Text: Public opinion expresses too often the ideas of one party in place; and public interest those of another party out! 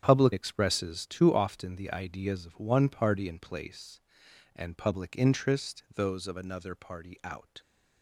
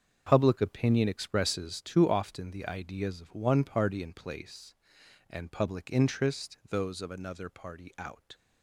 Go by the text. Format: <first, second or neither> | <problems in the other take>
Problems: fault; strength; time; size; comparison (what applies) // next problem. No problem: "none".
second | starts louder than the rest; strong; until 1.0 s; 8.5 dB; also in the second // skips "opinion"; at 0.3 s